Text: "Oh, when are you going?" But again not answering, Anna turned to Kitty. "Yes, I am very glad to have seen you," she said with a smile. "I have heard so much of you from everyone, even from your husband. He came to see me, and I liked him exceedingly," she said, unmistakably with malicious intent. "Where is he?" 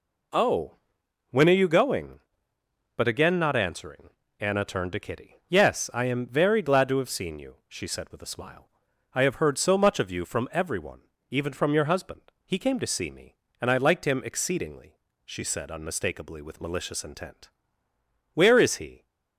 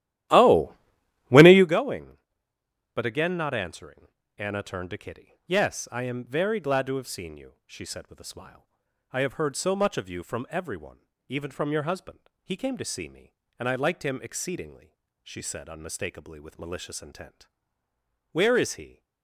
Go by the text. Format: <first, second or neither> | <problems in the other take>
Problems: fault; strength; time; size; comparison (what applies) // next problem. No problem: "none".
first | starts louder than the rest; strong; until 1.7 s; 13.5 dB